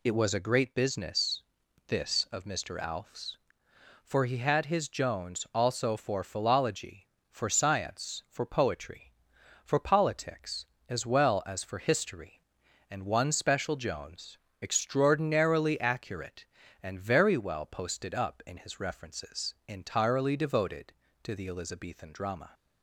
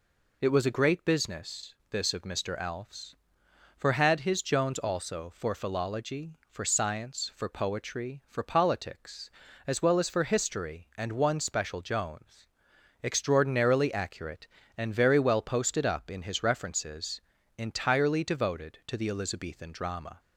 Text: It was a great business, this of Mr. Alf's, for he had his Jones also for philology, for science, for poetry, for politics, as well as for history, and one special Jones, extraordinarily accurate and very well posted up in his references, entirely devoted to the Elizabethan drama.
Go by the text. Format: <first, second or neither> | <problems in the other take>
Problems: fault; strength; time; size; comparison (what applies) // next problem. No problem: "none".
first | skips "he"; at 3.9 s